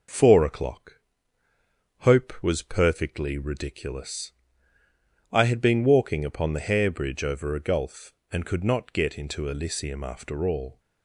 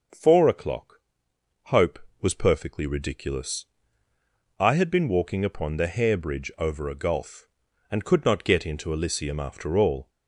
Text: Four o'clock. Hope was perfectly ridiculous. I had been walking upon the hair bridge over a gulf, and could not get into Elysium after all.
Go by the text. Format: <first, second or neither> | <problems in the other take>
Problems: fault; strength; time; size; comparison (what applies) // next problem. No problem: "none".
neither | none